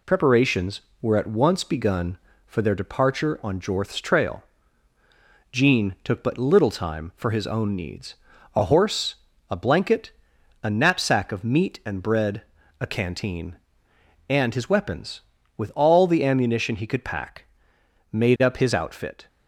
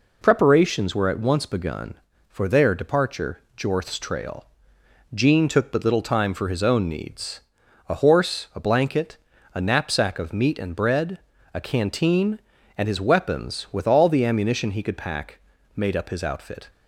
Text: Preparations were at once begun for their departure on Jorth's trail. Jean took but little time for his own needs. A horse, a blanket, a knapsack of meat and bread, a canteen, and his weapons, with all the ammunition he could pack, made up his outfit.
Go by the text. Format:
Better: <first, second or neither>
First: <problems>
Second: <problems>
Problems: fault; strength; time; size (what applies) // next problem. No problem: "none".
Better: first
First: none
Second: skips "on"; at 3.4 s